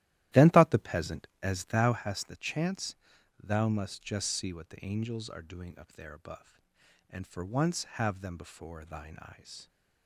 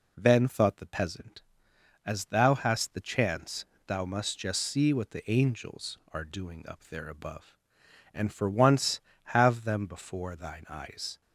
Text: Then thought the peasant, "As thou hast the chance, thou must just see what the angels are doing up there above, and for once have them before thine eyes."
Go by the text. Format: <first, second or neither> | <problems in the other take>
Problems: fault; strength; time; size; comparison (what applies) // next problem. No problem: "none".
second | starts louder than the rest; strong; until 2.1 s; 14 dB